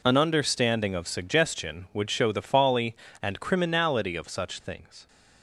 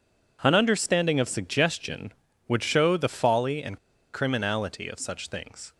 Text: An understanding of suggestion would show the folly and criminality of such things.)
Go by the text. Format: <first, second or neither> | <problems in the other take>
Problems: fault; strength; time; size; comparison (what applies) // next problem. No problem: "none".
first | pauses between "and" and "criminality"; slight; at 3.7 s; 0.35 s long